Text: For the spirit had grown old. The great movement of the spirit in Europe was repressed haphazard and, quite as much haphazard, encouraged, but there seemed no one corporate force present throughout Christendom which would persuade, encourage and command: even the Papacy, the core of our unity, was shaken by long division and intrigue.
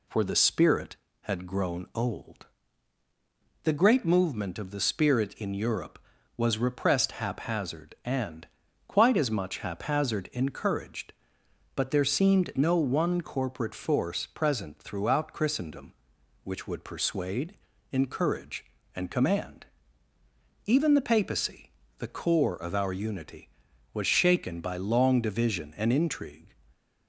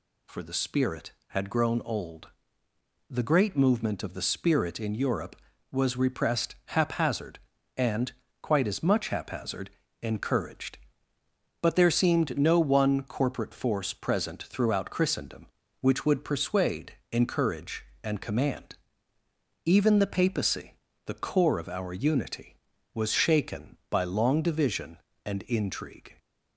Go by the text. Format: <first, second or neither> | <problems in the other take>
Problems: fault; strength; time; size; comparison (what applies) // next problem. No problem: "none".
neither | none